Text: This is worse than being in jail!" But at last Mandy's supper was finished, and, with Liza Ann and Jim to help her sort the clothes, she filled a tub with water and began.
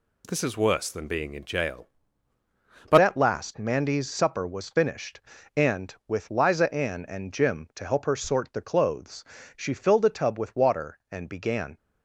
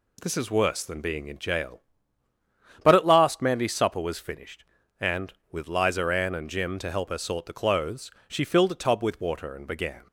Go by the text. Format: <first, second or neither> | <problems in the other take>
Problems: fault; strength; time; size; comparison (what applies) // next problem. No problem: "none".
second | changes voice at "at"; from 3.0 s on; 8.7 s long